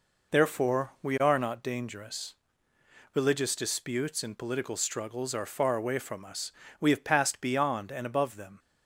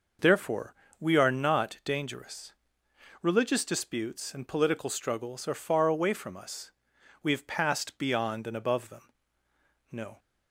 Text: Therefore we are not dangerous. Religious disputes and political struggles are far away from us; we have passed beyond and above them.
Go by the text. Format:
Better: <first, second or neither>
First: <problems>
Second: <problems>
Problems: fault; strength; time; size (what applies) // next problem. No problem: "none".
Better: first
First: none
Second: pauses between "Therefore" and "we"; slight; at 0.7 s; 0.24 s long // goes on to say "No"; slight; from 9.9 s on; 0.26 s long